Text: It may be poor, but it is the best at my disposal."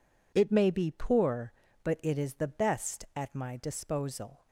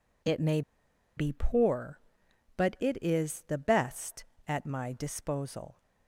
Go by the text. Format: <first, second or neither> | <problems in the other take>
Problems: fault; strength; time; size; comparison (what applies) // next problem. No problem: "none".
first | pauses between "may" and "be"; noticeable; at 0.6 s; 0.56 s long